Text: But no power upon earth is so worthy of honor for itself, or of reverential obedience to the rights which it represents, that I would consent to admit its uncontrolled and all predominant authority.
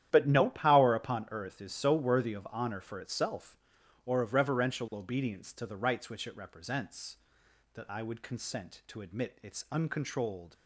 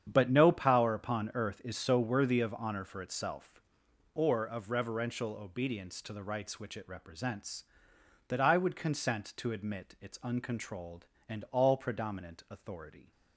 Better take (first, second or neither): second